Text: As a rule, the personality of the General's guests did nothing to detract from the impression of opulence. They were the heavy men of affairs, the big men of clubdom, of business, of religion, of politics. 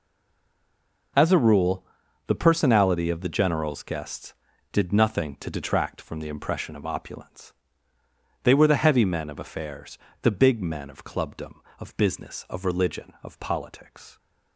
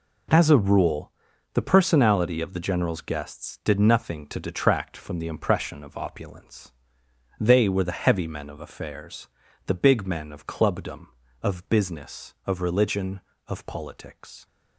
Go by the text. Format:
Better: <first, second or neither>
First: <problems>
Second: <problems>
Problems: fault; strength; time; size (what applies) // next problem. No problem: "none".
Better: second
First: stays silent before the first word; until 1.1 s; 1.1 s long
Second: none